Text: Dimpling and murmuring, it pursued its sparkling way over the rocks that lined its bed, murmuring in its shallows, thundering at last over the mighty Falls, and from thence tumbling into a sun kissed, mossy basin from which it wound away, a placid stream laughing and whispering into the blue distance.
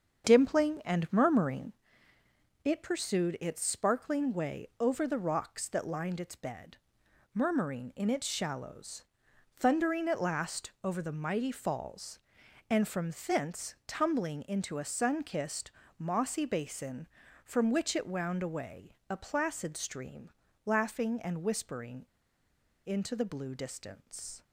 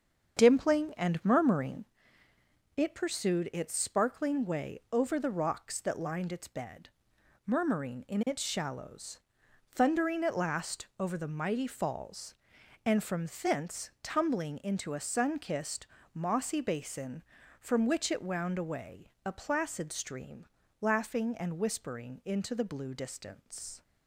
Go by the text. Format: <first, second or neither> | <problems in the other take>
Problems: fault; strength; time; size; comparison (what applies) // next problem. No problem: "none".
second | starts louder than the rest; strong; until 1.3 s; 7 dB; strong in the second // pauses between "from" and "thence"; slight; at 13.1 s; 0.16 s long; slight in the second // pauses between "stream" and "laughing"; slight; at 20.3 s; 0.34 s long; slight in the second // pauses between "whispering" and "into"; noticeable; at 22.0 s; 0.82 s long